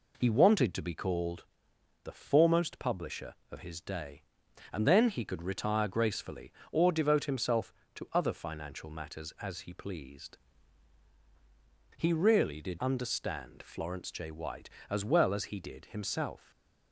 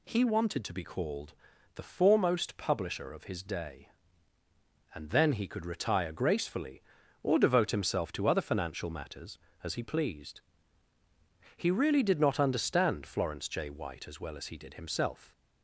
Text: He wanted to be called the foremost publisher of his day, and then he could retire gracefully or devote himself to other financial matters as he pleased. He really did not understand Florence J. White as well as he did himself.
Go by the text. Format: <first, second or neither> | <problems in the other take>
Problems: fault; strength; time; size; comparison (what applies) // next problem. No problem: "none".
second | pauses between "called" and "the"; noticeable; at 1.4 s; 0.60 s long; also in the second // skips "not"; at 12.7 s // stays silent after the last word; slight; from 16.3 s on; 0.6 s long